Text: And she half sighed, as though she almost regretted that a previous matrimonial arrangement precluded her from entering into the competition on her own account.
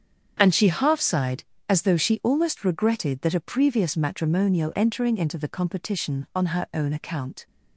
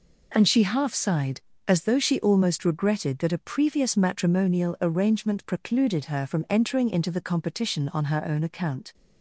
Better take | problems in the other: second | starts louder than the rest; strong; until 1.4 s; 7.5 dB // skips "arrangement precluded her from"; at 4.7 s

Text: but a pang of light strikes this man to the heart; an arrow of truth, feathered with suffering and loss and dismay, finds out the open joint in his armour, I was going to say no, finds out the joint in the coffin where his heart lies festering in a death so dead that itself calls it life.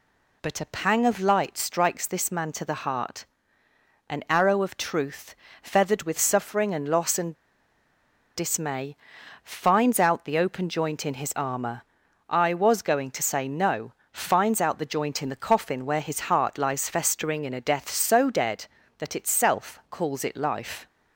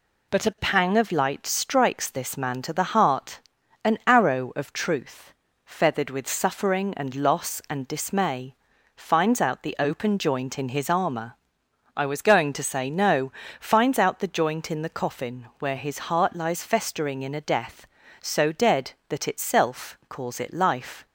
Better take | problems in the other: second | pauses between "and" and "dismay"; at 7.3 s; 1.0 s long

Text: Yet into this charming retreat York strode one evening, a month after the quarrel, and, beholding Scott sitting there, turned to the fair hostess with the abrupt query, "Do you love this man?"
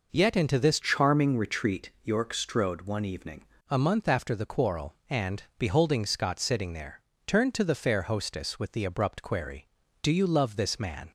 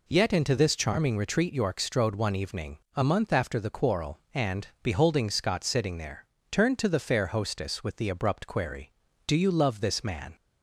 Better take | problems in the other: second | changes voice from "charming" to "evening"; from 0.7 to 3.4 s; 2.7 s long // pauses between "retreat" and "York"; slight; at 1.8 s; 0.16 s long

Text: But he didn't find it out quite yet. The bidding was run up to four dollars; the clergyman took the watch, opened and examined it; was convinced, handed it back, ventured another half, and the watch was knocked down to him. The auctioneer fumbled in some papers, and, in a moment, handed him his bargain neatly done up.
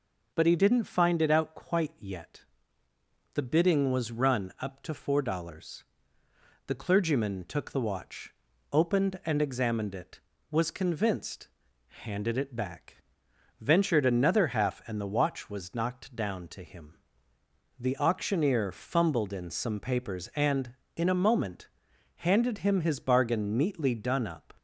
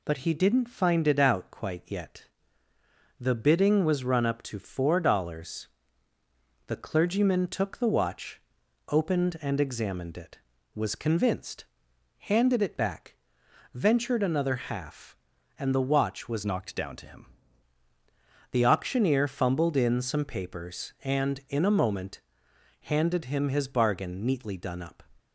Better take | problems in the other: first | changes voice from "knocked" to "him"; from 16.4 to 17.2 s; 0.8 s long

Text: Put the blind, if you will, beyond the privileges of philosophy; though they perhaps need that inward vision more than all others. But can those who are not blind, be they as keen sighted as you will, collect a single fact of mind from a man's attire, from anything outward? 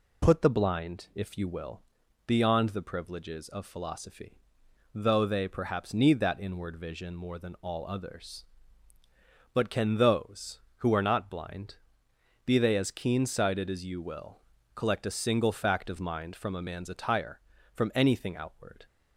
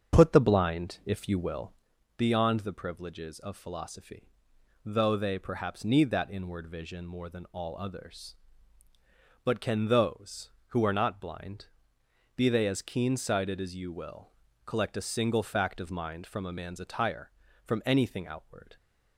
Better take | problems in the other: first | starts louder than the rest; strong; until 1.9 s; 7.5 dB

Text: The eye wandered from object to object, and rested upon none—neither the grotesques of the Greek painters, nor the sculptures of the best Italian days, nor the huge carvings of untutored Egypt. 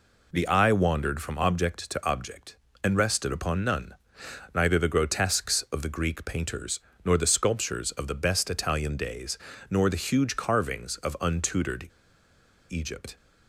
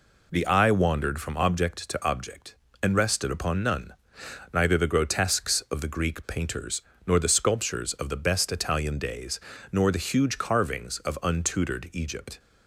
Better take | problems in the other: second | pauses between "untutored" and "Egypt"; noticeable; at 11.8 s; 0.80 s long

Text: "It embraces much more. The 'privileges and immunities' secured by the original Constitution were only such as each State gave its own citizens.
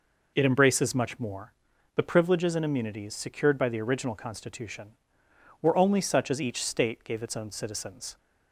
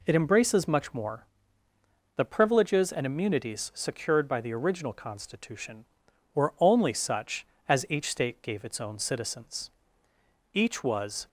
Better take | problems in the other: first | goes on to say "Each was"; noticeable; from 10.5 s on; 0.74 s long

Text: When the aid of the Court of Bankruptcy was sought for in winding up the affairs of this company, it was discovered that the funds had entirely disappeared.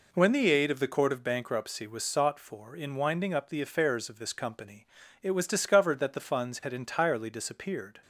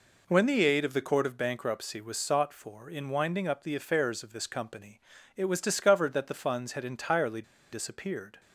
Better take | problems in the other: first | pauses between "entirely" and "disappeared"; slight; at 7.4 s; 0.29 s long

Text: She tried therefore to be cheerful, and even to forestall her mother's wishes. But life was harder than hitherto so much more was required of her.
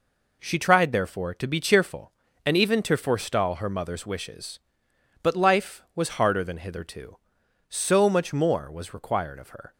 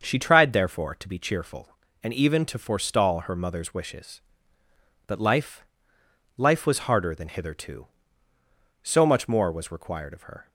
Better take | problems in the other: first | starts louder than the rest; until 1.0 s; 6.5 dB // says "life" twice; at 6.3 s

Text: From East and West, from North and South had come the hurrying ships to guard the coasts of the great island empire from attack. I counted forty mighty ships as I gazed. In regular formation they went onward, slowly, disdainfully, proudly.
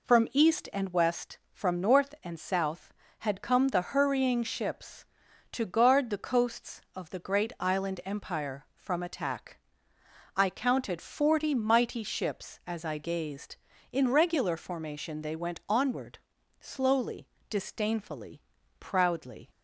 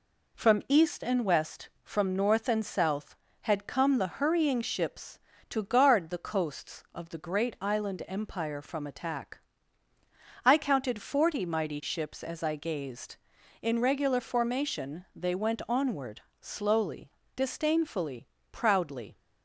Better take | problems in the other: neither | none

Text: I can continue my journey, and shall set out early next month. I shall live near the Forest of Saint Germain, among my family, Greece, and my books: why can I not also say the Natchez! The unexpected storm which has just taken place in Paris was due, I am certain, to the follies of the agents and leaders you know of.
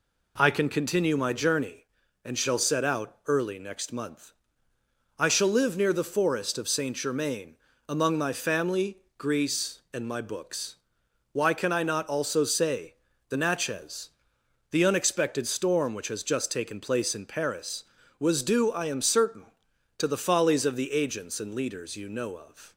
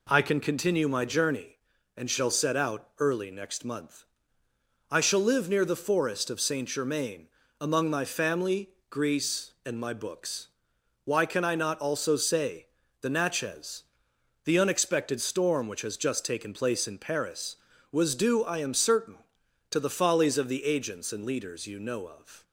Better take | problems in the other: neither | pauses between "say" and "the"; slight; the same in both

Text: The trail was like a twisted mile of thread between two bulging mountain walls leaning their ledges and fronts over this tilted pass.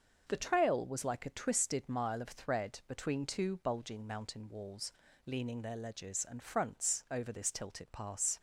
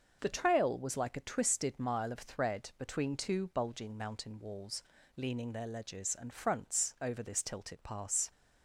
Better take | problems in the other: neither | starts louder than the rest; noticeable; the same in both // pauses between "walls" and "leaning"; slight; the same in both

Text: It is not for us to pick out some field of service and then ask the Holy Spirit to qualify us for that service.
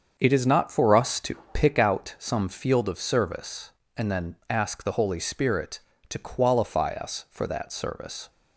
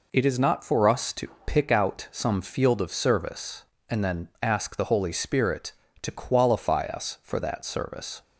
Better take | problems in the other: second | starts louder than the rest; until 2.1 s; 7 dB // pauses between "to" and "pick"; slight; at 1.3 s; 0.18 s long; slight in the second

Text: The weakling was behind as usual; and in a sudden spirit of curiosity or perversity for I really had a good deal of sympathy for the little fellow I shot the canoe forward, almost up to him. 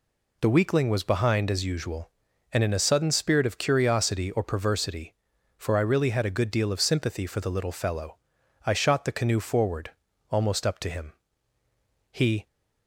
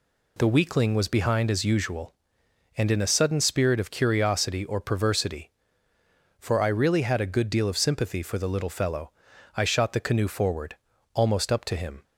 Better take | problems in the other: second | pauses between "fellow" and "I"; noticeable; at 8.1 s; 0.46 s long; noticeable in the second // goes on to say "He"; slight; from 12.1 s on; 0.34 s long

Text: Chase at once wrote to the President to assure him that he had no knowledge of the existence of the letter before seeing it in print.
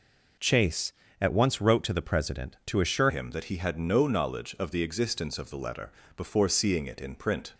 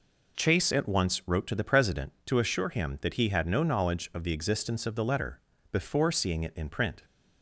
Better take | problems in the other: second | changes voice at "him"; from 3.0 s on; 4.5 s long // pauses between "letter" and "before"; slight; at 5.8 s; 0.28 s long; slight in the second

